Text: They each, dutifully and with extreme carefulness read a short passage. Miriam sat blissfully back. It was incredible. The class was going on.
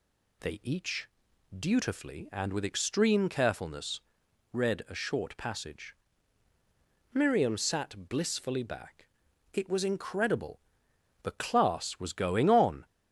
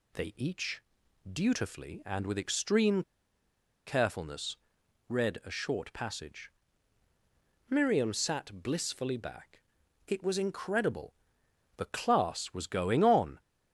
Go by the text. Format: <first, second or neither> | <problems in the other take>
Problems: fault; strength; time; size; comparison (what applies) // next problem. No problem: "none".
first | pauses between "extreme" and "carefulness"; noticeable; at 3.0 s; 0.84 s long // pauses between "carefulness" and "read"; noticeable; at 4.5 s; 0.52 s long; noticeable in the first